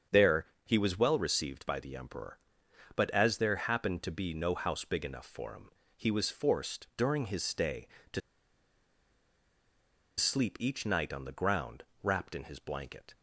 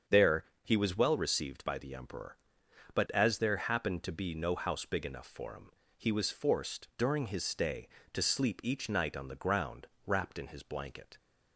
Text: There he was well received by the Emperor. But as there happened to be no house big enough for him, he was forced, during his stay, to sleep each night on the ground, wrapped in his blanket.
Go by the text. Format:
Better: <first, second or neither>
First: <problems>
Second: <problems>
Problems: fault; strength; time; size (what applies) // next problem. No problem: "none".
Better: second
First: starts louder than the rest; strong; until 1.2 s; 7.5 dB // pauses between "There" and "he"; slight; at 0.4 s; 0.18 s long // pauses between "to" and "sleep"; strong; at 8.2 s; 1.9 s long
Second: starts louder than the rest; strong; until 1.2 s; 7 dB // pauses between "There" and "he"; slight; at 0.4 s; 0.18 s long